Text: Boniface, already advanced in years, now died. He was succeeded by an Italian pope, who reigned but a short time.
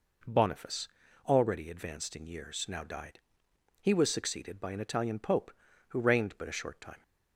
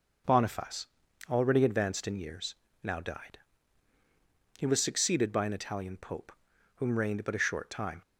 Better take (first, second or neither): first